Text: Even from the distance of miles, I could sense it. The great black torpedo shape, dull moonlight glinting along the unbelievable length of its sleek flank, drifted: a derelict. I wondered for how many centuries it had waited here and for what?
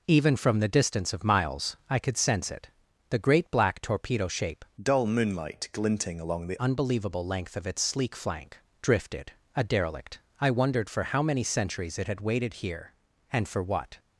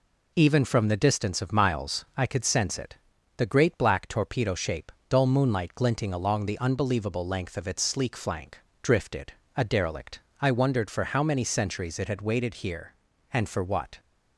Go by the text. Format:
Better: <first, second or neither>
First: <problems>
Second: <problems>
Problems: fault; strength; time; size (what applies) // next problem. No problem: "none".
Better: second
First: changes voice from "dull" to "the"; from 4.8 to 6.6 s; 1.8 s long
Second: none